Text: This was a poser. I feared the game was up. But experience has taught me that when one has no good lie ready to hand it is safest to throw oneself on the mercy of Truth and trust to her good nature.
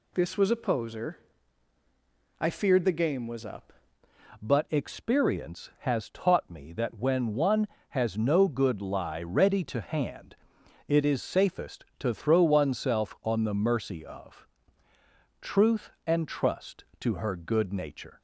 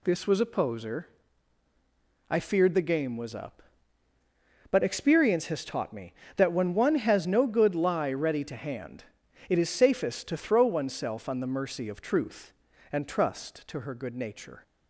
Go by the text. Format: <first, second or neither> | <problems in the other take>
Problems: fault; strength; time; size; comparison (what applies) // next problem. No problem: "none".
second | changes voice at "But"; from 4.4 s on; 13.8 s long // pauses between "hand" and "it"; noticeable; at 10.3 s; 0.50 s long; also in the second // pauses between "of" and "Truth"; noticeable; at 14.4 s; 0.94 s long